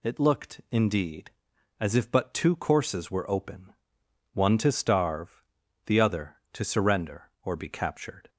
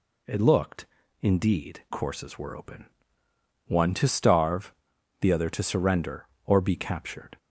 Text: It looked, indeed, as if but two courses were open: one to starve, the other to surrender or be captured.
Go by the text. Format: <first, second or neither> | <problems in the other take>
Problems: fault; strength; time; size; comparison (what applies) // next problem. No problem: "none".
first | skips "as if but two"; at 1.8 s